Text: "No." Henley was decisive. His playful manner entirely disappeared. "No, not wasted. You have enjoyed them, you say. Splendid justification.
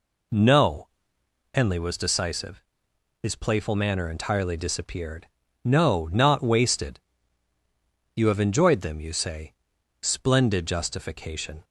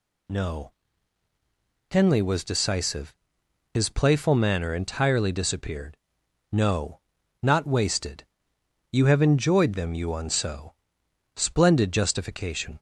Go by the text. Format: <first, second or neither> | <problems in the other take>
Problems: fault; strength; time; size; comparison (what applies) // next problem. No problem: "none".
first | says "unso" for "say"; at 10.0 s